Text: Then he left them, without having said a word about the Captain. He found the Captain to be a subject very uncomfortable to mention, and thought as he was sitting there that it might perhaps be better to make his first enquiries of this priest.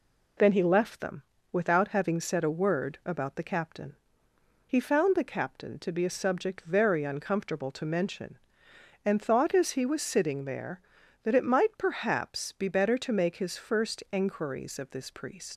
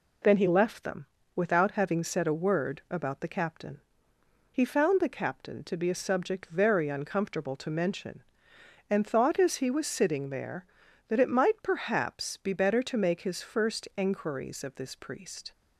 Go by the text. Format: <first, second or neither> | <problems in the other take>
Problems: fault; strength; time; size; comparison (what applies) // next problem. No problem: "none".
second | leaves "priest" unfinished; at 15.5 s; 95 ms